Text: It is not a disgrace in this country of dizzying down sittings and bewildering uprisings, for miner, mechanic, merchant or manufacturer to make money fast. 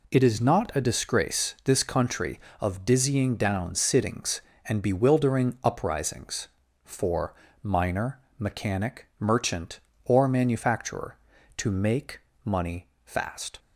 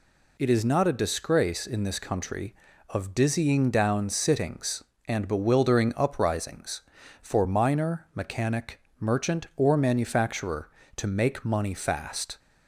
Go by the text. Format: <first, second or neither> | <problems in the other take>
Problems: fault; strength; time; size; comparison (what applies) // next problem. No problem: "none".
second | skips "in"; at 1.5 s // pauses between "for" and "miner"; slight; at 7.3 s; 0.30 s long // pauses between "make" and "money"; slight; at 12.2 s; 0.24 s long // pauses between "money" and "fast"; slight; at 12.8 s; 0.20 s long